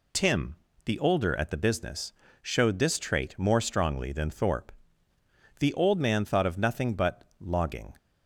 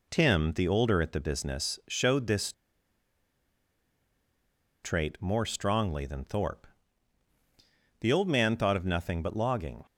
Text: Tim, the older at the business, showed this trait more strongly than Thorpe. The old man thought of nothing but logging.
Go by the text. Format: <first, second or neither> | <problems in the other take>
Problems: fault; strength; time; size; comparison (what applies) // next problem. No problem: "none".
first | pauses between "this" and "trait"; strong; at 2.5 s; 2.3 s long